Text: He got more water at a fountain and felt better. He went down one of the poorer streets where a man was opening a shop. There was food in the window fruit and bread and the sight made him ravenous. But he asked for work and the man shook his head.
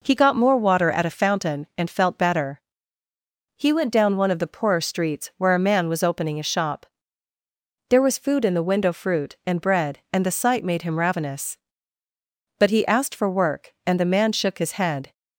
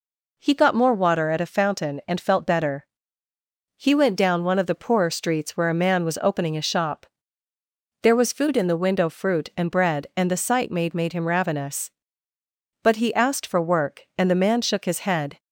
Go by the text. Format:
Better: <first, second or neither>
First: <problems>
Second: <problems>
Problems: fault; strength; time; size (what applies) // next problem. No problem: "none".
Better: first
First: none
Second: says "made" twice; at 10.9 s